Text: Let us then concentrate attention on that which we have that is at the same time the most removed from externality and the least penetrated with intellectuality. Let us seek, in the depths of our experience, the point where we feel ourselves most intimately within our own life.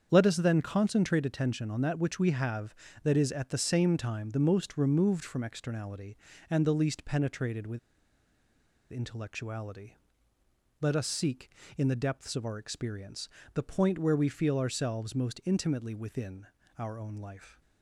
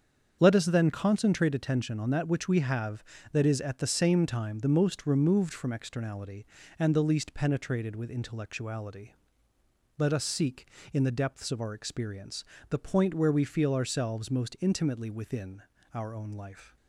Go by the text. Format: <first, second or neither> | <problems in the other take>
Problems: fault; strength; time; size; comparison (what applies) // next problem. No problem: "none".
second | starts louder than the rest; strong; until 1.1 s; 7.5 dB; strong in the second // pauses between "with" and "intellectuality"; at 7.7 s; 1.1 s long // pauses between "within" and "our"; slight; at 16.4 s; 0.32 s long; slight in the second